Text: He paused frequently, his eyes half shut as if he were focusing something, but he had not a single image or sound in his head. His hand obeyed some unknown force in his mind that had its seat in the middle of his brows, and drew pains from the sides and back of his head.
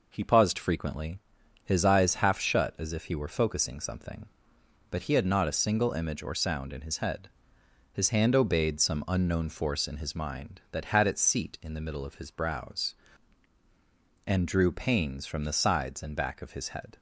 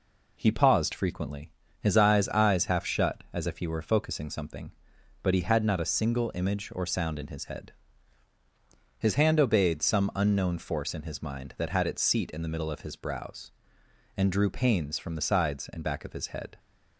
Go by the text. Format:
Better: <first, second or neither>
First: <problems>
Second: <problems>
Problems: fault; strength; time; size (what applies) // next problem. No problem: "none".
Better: first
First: none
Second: says "eyes" twice; at 2.2 s